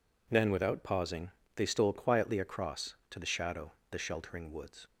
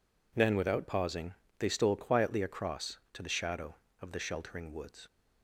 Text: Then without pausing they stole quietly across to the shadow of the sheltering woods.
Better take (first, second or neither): second